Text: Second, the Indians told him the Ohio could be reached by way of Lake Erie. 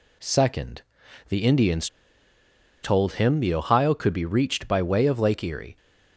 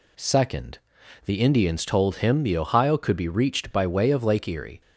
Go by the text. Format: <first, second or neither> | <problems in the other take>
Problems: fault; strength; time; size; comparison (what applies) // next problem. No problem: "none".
second | pauses between "Indians" and "told"; noticeable; at 1.8 s; 0.96 s long